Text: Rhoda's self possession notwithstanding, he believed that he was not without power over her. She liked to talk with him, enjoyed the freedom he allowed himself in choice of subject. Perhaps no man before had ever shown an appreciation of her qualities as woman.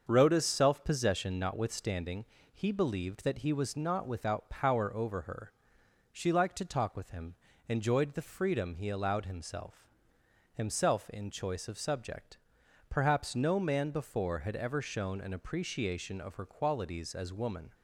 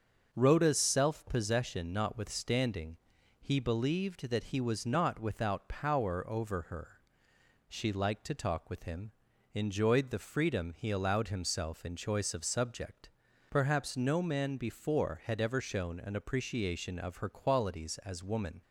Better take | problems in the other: second | starts louder than the rest; until 1.0 s; 6.5 dB; also in the second // says "himself" twice; at 10.5 s

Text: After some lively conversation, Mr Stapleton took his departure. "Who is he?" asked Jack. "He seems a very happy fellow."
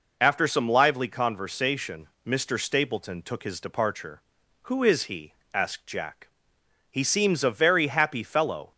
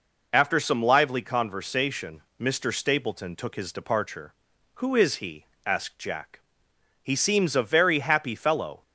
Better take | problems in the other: neither | none

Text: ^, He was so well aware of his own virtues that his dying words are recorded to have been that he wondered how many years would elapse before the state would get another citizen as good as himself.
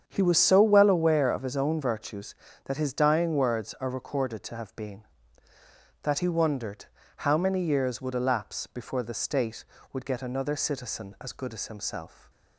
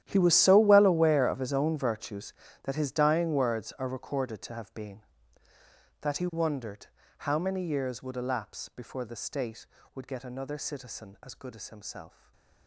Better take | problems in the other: first | gets quieter; strong; throughout; 17.5 dB // starts louder than the rest; strong; until 1.0 s; 11 dB; strong in the first // pauses between "wondered" and "how"; slight; at 6.8 s; 0.32 s long; slight in the first // stays silent after the last word; slight; from 12.0 s on; 0.6 s long

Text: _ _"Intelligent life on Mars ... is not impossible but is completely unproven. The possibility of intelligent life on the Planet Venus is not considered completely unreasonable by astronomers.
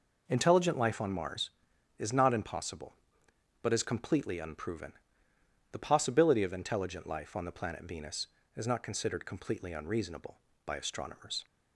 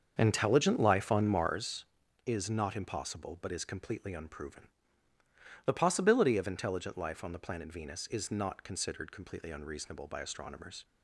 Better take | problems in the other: first | starts louder than the rest; until 1.6 s; 7 dB

